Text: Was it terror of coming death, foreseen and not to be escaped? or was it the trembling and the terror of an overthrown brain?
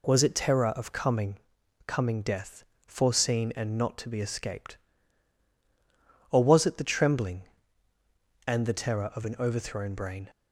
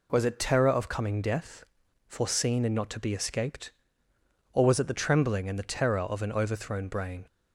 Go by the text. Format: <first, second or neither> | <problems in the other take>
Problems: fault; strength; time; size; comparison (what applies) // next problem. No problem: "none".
second | says "coming" twice; at 1.8 s